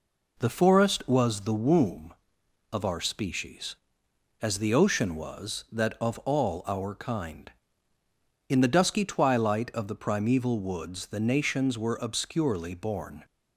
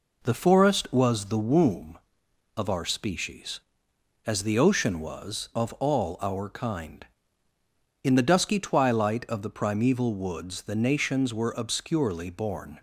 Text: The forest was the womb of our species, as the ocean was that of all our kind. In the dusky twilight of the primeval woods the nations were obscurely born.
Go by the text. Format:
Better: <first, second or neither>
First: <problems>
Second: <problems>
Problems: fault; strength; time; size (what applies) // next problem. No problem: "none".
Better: first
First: none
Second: skips "that"; at 5.5 s